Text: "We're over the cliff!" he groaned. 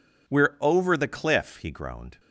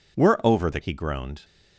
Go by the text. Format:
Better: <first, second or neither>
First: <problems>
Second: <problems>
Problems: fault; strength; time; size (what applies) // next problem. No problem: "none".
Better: first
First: none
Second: skips "cliff"; at 0.8 s